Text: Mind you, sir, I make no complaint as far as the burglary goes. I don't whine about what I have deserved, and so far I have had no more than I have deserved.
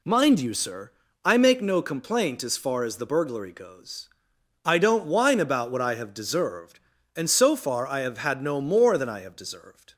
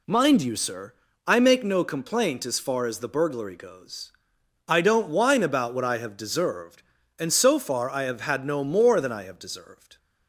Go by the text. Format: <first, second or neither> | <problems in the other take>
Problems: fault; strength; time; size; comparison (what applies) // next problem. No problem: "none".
neither | none